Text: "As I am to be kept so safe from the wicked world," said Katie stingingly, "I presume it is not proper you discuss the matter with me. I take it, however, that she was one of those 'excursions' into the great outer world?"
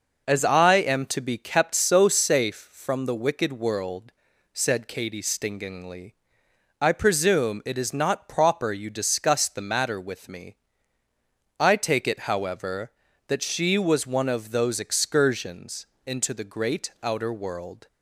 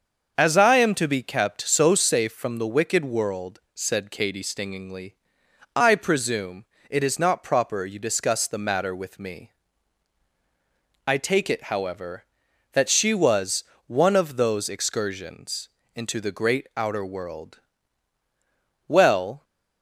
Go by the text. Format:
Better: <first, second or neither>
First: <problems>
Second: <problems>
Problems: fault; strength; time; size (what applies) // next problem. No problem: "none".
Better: first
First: pauses between "excursions" and "into"; slight; at 15.8 s; 0.18 s long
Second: starts louder than the rest; until 1.3 s; 6.5 dB // pauses between "presume" and "it"; slight; at 6.6 s; 0.26 s long // pauses between "was" and "one"; slight; at 13.6 s; 0.24 s long // pauses between "excursions" and "into"; slight; at 15.6 s; 0.28 s long // goes on to say "Well"; from 18.8 s on; 0.56 s long